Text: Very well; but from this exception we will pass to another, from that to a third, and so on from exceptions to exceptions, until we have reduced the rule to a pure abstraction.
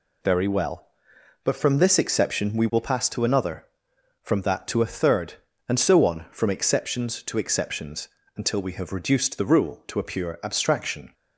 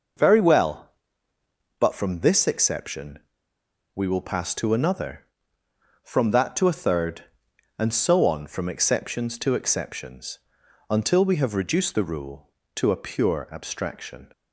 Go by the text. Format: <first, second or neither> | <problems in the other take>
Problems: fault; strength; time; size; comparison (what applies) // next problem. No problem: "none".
first | pauses between "exception" and "we"; noticeable; at 3.1 s; 0.74 s long